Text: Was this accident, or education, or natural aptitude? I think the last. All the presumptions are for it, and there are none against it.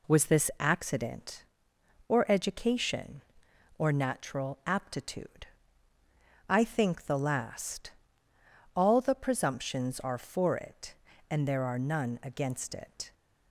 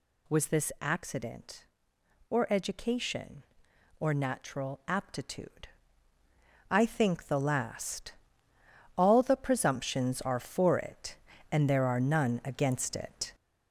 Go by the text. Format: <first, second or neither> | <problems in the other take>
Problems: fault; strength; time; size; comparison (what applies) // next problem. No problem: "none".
first | gets louder; noticeable; throughout; 5 dB